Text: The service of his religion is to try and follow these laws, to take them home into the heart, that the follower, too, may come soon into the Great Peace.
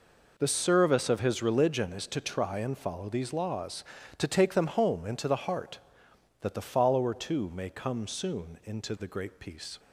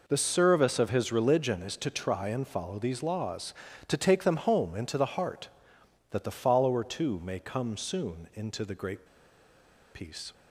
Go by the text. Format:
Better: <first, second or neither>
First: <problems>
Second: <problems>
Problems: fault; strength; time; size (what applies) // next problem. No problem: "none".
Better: first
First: none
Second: pauses between "Great" and "Peace"; noticeable; at 9.0 s; 0.87 s long